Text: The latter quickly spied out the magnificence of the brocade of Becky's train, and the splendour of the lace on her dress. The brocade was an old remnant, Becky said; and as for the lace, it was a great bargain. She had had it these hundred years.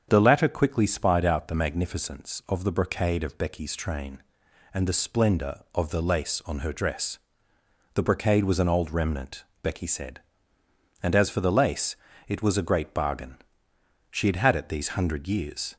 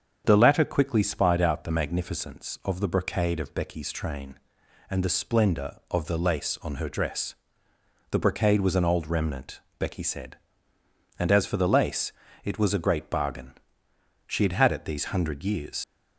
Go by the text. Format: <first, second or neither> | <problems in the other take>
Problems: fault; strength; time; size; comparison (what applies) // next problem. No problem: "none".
first | starts louder than the rest; strong; until 1.2 s; 7.5 dB; strong in the first // leaves "years" unfinished; at 15.8 s; 80 ms